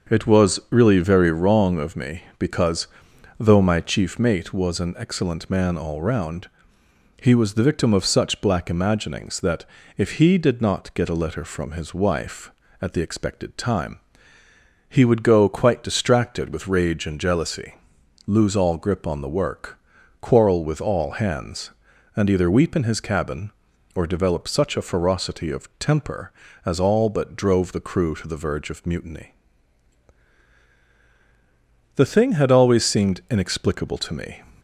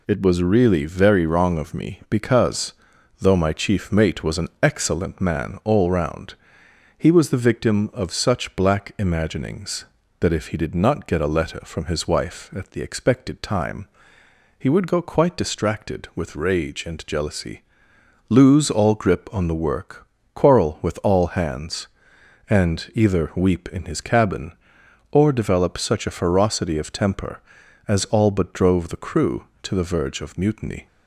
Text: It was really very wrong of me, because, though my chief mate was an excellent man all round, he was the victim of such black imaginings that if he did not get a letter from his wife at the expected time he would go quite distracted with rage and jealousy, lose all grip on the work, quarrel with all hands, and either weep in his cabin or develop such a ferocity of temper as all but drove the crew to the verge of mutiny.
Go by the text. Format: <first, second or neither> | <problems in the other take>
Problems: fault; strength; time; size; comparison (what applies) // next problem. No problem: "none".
second | starts louder than the rest; until 1.2 s; 6.5 dB // pauses between "that" and "if"; slight; at 9.6 s; 0.32 s long // pauses between "time" and "he"; noticeable; at 13.9 s; 0.90 s long; noticeable in the second // goes on to say "The thing had always seemed inexplicable to me"; strong; from 31.9 s on; 2.4 s long